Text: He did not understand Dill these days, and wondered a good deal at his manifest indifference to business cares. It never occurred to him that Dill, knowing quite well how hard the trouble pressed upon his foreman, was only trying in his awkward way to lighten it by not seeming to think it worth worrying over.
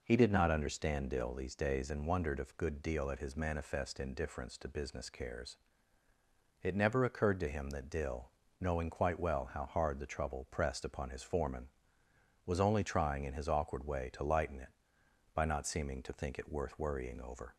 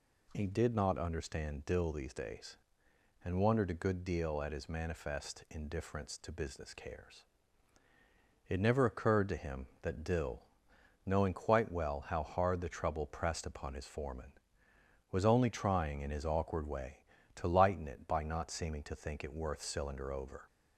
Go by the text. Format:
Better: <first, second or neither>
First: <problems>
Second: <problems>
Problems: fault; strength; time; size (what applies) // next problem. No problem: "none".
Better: first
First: none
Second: says "cylinder" for "worrying"; at 19.6 s